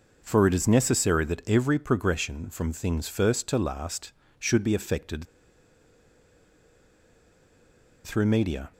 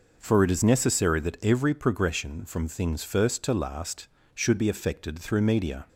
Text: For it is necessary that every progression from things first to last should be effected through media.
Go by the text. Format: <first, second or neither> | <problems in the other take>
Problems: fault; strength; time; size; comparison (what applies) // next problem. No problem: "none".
second | pauses between "effected" and "through"; strong; at 5.2 s; 2.8 s long